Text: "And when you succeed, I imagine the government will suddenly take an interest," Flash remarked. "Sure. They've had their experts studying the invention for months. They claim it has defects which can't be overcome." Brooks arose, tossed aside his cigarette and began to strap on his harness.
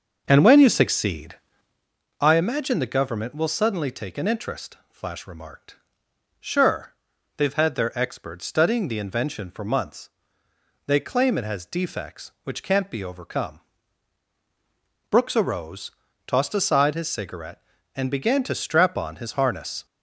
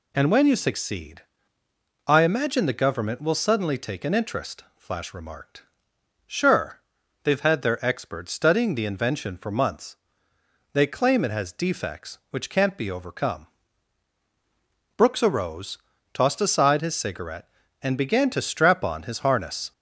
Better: second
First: starts louder than the rest; until 1.9 s; 6.5 dB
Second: none

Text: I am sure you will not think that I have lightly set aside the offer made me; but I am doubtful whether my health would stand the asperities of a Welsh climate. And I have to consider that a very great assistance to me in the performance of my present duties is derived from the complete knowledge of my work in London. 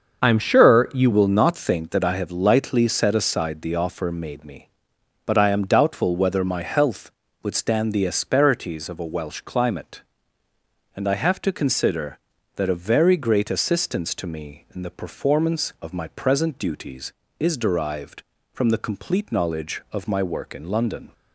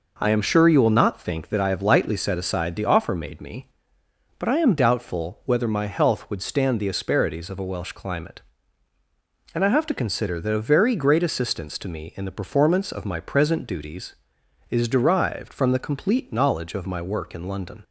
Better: second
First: starts louder than the rest; until 1.2 s; 6.5 dB // changes voice at "will"; from 1.1 s on; 20.0 s long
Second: none

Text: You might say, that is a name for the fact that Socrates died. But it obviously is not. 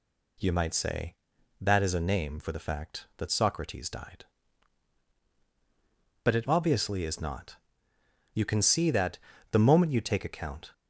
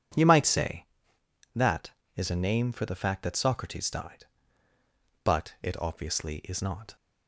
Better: second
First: goes on to say "You can see that the moment you take account"; strong; from 8.3 s on; 2.3 s long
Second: none

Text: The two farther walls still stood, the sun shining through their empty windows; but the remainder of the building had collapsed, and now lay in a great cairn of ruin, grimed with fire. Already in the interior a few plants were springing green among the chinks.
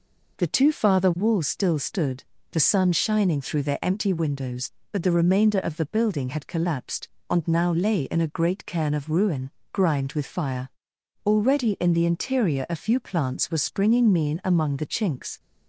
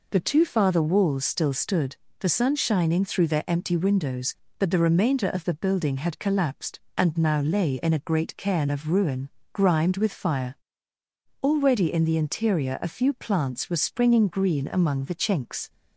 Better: second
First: says "mean" for "green"; at 14.1 s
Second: none

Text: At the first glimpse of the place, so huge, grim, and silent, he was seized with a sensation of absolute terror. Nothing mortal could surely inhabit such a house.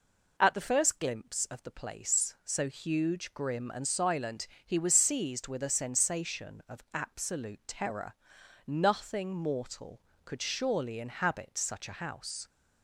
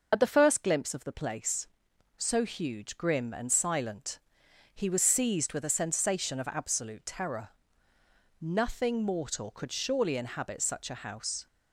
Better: first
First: none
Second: loses the start of "At"; at 0.1 s; 50 ms

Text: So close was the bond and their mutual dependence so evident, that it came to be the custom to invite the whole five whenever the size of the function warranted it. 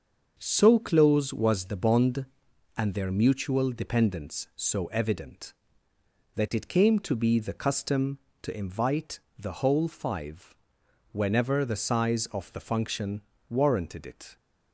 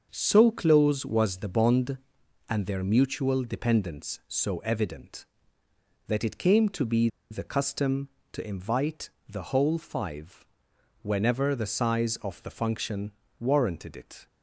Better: first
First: starts louder than the rest; until 1.3 s; 6.5 dB // pauses between "invite" and "the"; slight; at 9.2 s; 0.18 s long // pauses between "five" and "whenever"; noticeable; at 10.5 s; 0.58 s long // pauses between "function" and "warranted"; slight; at 13.2 s; 0.30 s long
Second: starts louder than the rest; until 1.1 s; 6.5 dB // pauses between "be" and "the"; slight; at 7.0 s; 0.22 s long // pauses between "invite" and "the"; slight; at 9.1 s; 0.18 s long // pauses between "five" and "whenever"; noticeable; at 10.4 s; 0.58 s long // pauses between "function" and "warranted"; slight; at 13.1 s; 0.30 s long

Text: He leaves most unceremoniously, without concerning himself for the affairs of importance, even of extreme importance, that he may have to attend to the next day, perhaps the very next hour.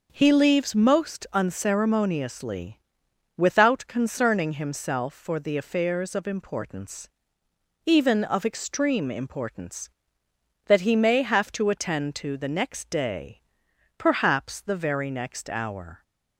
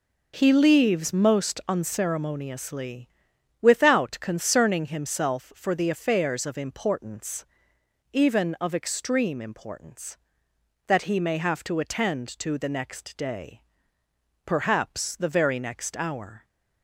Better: neither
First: none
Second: none

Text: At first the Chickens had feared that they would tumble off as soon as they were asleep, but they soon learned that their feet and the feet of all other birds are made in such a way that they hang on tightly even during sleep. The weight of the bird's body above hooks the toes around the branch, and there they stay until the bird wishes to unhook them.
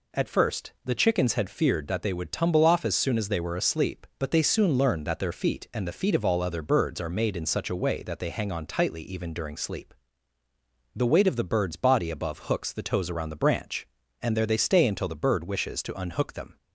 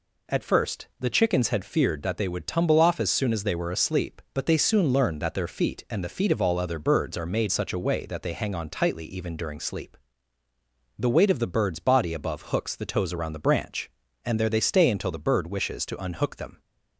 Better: first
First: none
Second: skips "in"; at 7.4 s

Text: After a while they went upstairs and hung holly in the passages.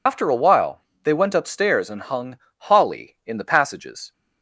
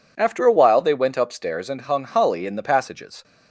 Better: second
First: loses the start of "After"; at 0.0 s; 75 ms // pauses between "while" and "they"; slight; at 0.8 s; 0.22 s long // pauses between "hung" and "holly"; slight; at 2.3 s; 0.22 s long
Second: none

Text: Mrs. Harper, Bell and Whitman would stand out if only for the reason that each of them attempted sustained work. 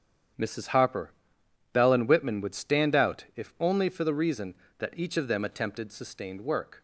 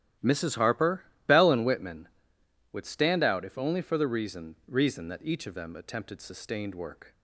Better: first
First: starts louder than the rest; strong; until 1.9 s; 8.5 dB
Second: starts louder than the rest; strong; until 1.4 s; 13 dB // says "reason" twice; at 4.6 s

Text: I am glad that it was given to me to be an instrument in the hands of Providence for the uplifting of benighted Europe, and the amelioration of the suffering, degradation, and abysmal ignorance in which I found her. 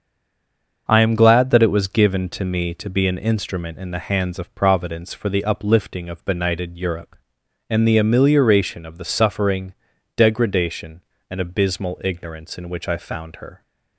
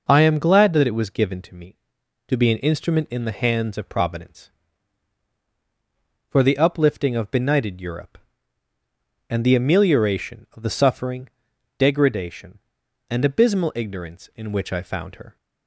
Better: second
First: stays silent before the first word; slight; until 0.8 s; 0.8 s long // starts louder than the rest; until 1.8 s; 6.5 dB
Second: none

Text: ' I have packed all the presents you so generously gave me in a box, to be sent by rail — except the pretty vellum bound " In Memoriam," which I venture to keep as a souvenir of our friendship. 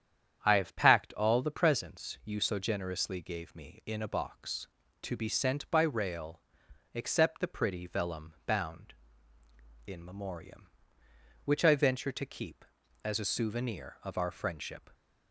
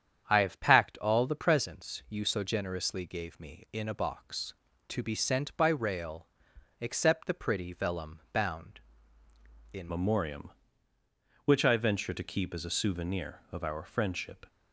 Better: first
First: starts louder than the rest; strong; until 1.4 s; 9 dB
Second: starts louder than the rest; strong; until 1.2 s; 9 dB // changes voice at "Memoriam"; from 9.8 s on; 4.6 s long

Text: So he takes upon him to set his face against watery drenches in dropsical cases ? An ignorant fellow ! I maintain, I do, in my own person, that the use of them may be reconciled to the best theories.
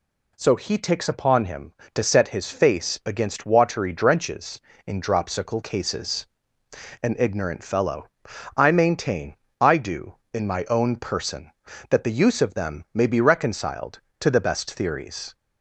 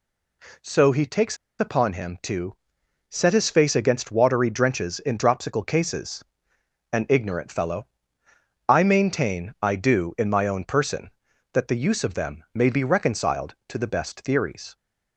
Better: first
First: none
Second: pauses between "takes" and "upon"; slight; at 1.3 s; 0.22 s long // pauses between "to" and "set"; noticeable; at 2.5 s; 0.54 s long

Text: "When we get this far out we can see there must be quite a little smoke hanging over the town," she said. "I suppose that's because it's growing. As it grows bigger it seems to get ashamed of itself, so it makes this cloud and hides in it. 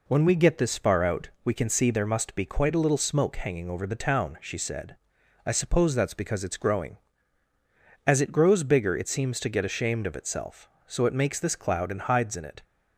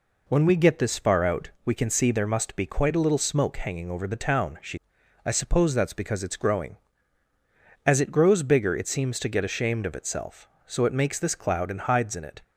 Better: first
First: none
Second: skips "said"; at 5.0 s

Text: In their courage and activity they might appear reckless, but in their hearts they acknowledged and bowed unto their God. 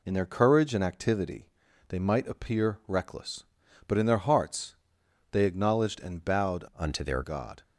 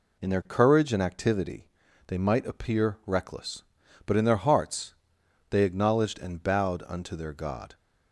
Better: second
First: pauses between "activity" and "they"; at 1.4 s; 0.42 s long // pauses between "hearts" and "they"; noticeable; at 4.7 s; 0.56 s long // changes voice from "unto" to "their"; from 6.7 to 7.2 s; 0.5 s long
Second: pauses between "activity" and "they"; at 1.6 s; 0.42 s long // pauses between "hearts" and "they"; noticeable; at 4.9 s; 0.56 s long

